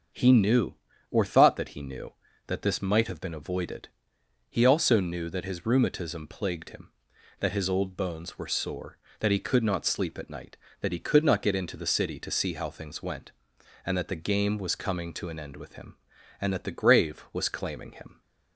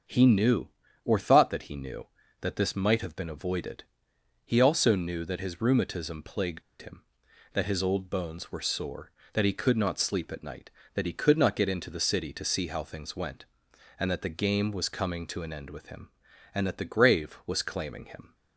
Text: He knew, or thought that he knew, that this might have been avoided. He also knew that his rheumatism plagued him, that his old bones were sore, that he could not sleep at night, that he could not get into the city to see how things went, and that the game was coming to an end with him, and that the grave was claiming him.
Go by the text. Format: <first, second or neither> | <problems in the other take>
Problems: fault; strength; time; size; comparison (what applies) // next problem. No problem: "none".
first | starts louder than the rest; until 1.4 s; 7 dB; also in the first // pauses between "plagued" and "him"; slight; at 6.6 s; 0.18 s long